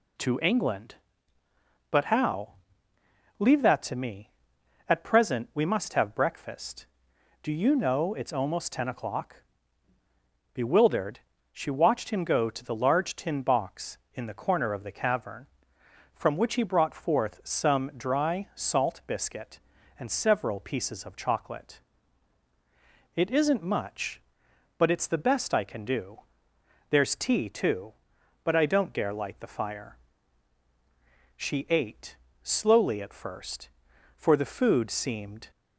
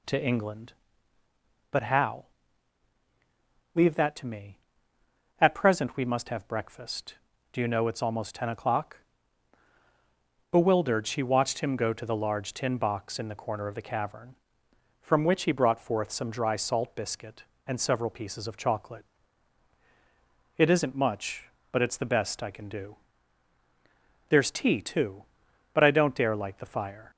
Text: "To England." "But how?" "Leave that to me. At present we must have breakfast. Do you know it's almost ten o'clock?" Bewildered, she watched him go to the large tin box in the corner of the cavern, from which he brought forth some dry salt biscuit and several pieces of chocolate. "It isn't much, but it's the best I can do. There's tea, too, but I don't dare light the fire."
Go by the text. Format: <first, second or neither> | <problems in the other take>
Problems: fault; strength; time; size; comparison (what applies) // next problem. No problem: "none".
second | goes on to say "She ate slowly at first for the food seemed"; strong; from 31.3 s on; 4.1 s long